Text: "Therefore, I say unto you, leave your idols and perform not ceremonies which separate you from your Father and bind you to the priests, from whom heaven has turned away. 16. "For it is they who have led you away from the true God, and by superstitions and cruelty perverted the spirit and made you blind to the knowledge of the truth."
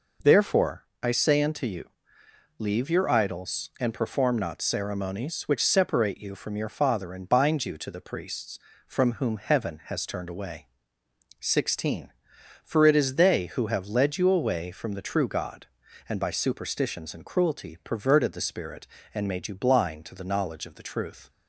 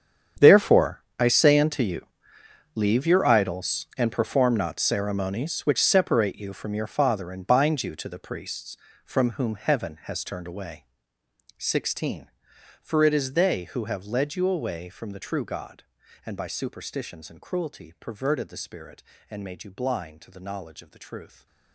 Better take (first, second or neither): first